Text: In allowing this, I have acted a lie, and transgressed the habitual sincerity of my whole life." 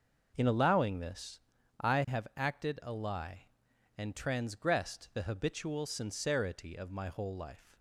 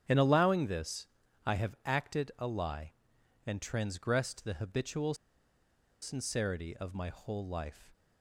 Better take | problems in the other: first | starts louder than the rest; strong; until 1.4 s; 10.5 dB // pauses between "habitual" and "sincerity"; noticeable; at 5.1 s; 0.87 s long

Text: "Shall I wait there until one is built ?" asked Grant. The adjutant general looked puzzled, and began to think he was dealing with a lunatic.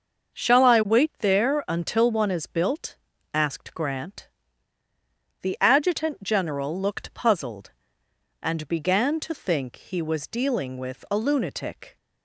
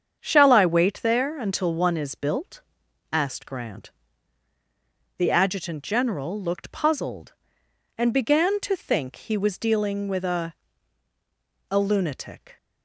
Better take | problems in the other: first | starts louder than the rest; strong; until 1.2 s; 7.5 dB; also in the first // says "a" twice; at 11.7 s

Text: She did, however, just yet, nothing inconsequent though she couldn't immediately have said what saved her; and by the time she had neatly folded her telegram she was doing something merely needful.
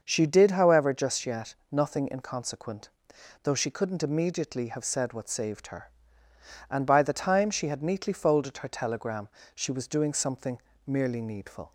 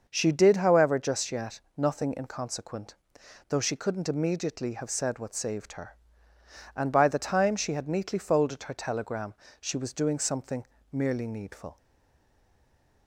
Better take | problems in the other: first | starts louder than the rest; until 1.0 s; 6.5 dB; also in the first // pauses between "inconsequent" and "though"; noticeable; at 2.9 s; 0.54 s long; noticeable in the first // pauses between "telegram" and "she"; slight; at 9.3 s; 0.26 s long; slight in the first // pauses between "something" and "merely"; slight; at 10.6 s; 0.28 s long; slight in the first // stays silent after the last word; noticeable; from 11.7 s on; 1.3 s long

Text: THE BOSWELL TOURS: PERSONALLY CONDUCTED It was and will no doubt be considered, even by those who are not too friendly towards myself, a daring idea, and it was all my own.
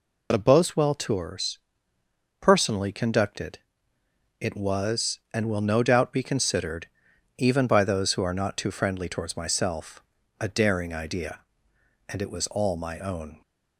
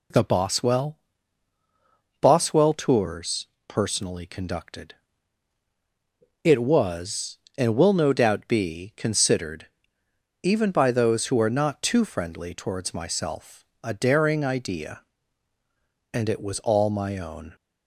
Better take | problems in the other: first | says "BOSWELL" twice; at 2.1 s // pauses between "CONDUCTED" and "It"; strong; at 4.9 s; 1.4 s long; noticeable in the first

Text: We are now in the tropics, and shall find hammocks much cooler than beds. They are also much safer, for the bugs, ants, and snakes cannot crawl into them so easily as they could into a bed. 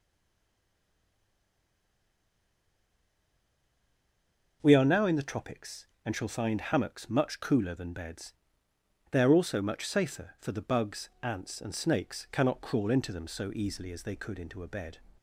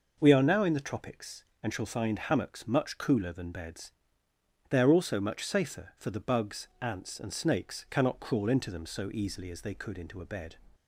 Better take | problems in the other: second | stays silent before the first word; strong; until 4.6 s; 4.6 s long

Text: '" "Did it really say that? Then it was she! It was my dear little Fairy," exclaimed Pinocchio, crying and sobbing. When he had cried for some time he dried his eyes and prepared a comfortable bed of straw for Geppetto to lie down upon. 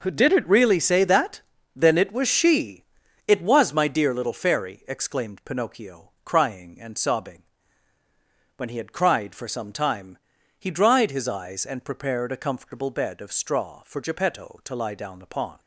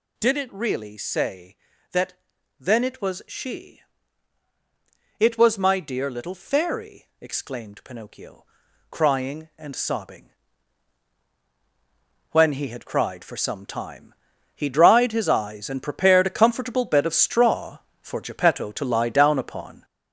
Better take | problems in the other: first | gets louder; noticeable; throughout; 6 dB // pauses between "time" and "he"; at 14.1 s; 0.40 s long; also in the first

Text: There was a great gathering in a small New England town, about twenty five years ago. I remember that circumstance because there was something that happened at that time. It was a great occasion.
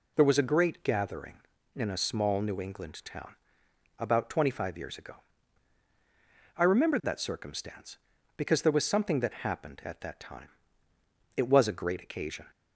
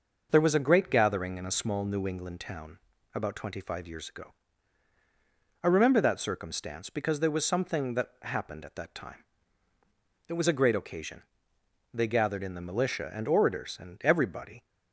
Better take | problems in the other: first | goes on to say "They gathered in the militia and orators and everybody"; strong; from 11.9 s on; 2.7 s long

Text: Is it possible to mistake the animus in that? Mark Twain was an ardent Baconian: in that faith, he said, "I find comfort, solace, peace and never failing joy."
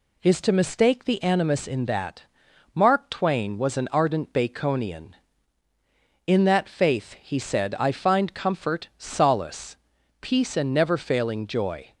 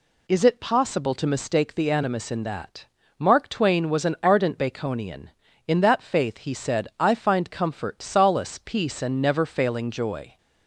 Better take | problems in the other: second | skips "it possible"; at 0.4 s

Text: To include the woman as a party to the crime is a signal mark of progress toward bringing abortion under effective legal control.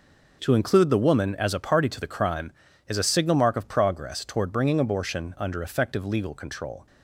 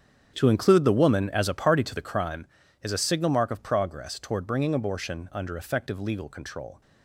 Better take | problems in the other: first | starts louder than the rest; strong; until 2.2 s; 8 dB

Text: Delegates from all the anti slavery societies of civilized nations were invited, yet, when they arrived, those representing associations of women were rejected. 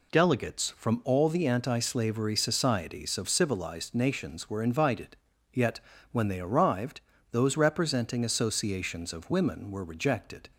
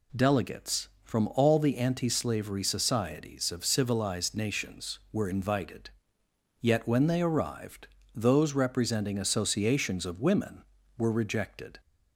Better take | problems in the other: neither | none

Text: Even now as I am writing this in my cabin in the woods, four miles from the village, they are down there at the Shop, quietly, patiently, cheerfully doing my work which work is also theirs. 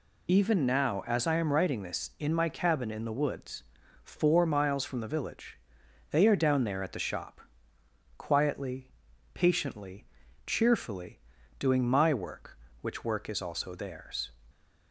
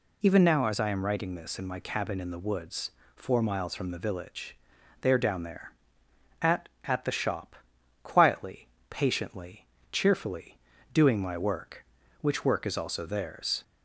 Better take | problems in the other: first | says "at" twice; at 6.8 s // pauses between "cheerfully" and "doing"; slight; at 10.5 s; 0.34 s long; also in the first

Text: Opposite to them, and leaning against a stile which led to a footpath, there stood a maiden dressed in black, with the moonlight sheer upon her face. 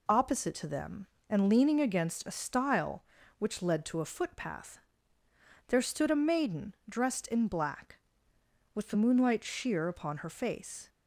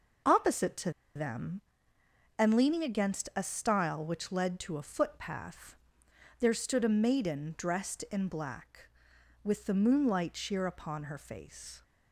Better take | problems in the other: first | pauses between "to" and "them"; slight; at 0.9 s; 0.23 s long

